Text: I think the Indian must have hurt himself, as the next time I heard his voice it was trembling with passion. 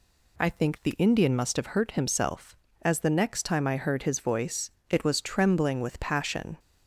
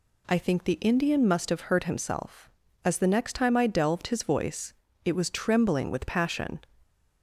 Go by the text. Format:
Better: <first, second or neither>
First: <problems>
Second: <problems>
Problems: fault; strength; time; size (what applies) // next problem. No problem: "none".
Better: first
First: pauses between "voice" and "it"; slight; at 4.6 s; 0.22 s long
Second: says "delved" for "heard"; at 3.6 s // pauses between "voice" and "it"; slight; at 4.7 s; 0.32 s long